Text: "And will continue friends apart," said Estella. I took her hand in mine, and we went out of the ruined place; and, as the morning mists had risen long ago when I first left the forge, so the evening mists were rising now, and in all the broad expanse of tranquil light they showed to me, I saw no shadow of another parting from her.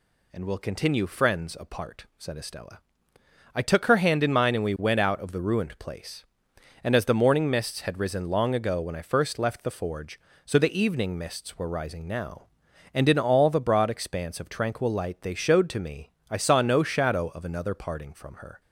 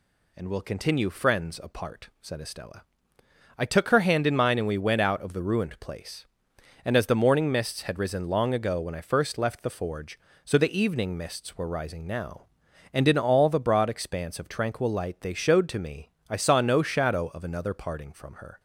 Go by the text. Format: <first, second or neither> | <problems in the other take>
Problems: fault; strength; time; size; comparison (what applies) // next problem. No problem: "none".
neither | none